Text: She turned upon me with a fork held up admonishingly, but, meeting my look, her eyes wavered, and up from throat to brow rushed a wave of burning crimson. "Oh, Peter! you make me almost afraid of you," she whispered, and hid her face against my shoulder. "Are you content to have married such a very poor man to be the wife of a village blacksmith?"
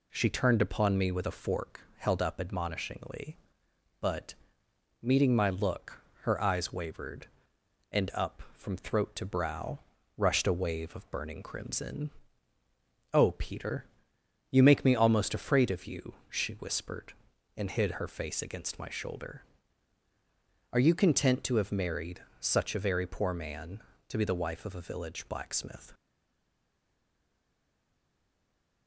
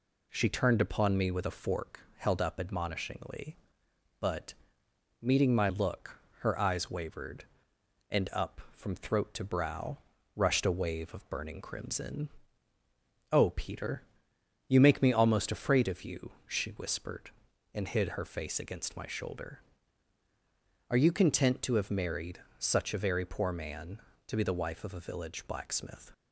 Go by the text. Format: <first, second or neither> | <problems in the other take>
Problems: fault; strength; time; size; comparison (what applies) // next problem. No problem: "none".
second | pauses between "fork" and "held"; slight; at 1.8 s; 0.16 s long; slight in the second // pauses between "brow" and "rushed"; at 9.7 s; 0.38 s long; also in the second // pauses between "married" and "such"; slight; at 22.2 s; 0.16 s long; slight in the second // stays silent after the last word; strong; from 25.9 s on; 2.9 s long